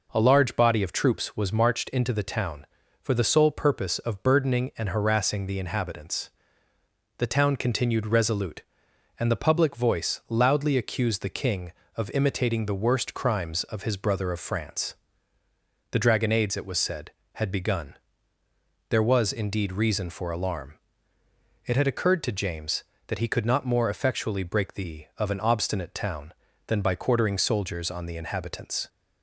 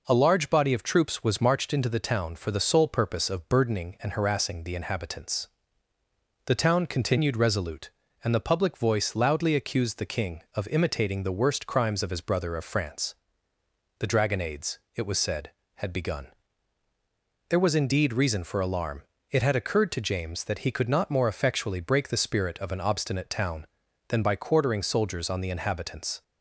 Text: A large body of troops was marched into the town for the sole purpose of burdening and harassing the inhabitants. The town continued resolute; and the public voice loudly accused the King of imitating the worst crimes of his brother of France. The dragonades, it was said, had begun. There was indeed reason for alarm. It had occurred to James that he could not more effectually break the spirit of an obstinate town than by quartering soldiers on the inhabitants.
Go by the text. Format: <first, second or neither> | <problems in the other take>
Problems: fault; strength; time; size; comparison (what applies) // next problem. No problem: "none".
second | skips "spirit"; at 25.1 s